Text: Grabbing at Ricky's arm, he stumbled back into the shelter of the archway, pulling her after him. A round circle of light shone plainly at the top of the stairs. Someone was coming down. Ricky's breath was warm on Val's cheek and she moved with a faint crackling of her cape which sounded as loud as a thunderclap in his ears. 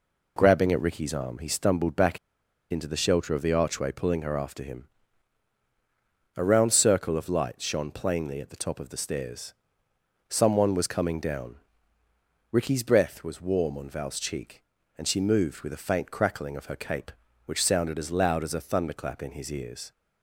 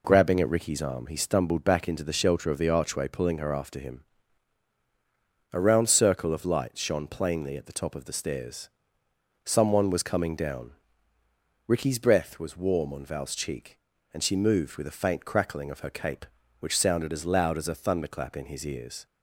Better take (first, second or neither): second